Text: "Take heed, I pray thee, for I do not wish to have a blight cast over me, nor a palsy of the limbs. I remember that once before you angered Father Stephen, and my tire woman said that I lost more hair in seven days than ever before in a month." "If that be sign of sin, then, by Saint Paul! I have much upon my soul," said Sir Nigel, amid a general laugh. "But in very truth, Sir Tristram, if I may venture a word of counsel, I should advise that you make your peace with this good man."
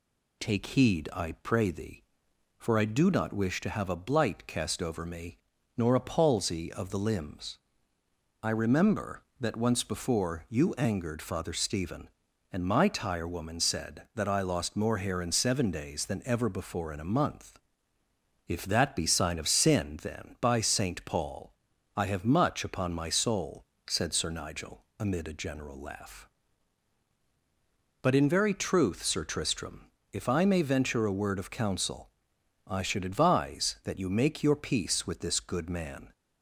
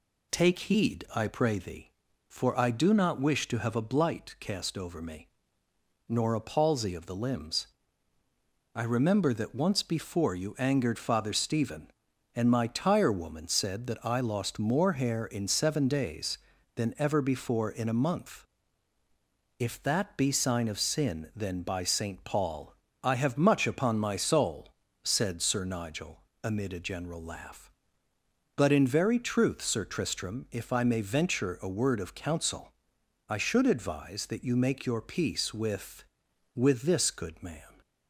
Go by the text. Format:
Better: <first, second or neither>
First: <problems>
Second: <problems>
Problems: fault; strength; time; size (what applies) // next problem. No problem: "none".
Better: first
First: none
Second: says "with" twice; at 36.5 s